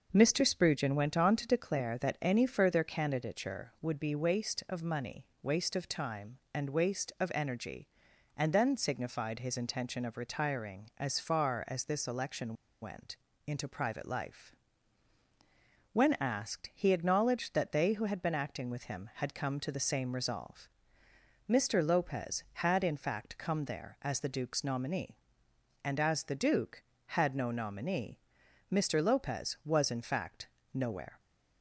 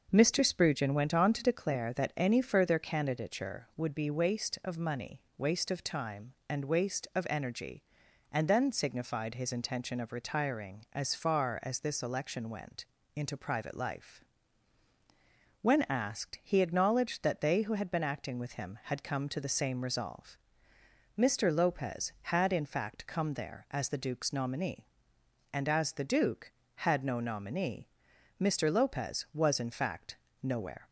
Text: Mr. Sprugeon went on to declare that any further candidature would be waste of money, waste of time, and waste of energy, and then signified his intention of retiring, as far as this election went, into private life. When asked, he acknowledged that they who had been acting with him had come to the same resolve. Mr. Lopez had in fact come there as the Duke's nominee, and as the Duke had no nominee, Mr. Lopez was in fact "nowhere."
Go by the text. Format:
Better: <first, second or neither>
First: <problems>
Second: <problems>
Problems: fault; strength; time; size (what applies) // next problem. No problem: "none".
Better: second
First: pauses between "election" and "went"; slight; at 12.5 s; 0.28 s long // pauses between "fact" and "nowhere"; slight; at 30.4 s; 0.26 s long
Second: pauses between "fact" and "nowhere"; slight; at 30.1 s; 0.26 s long